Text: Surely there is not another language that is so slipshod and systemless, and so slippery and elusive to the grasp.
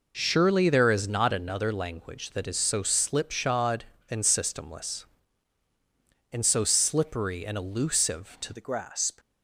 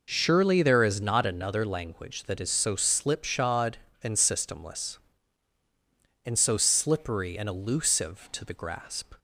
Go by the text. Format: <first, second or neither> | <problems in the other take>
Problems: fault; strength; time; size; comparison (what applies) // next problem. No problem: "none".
second | changes voice at "the"; from 8.5 s on; 0.6 s long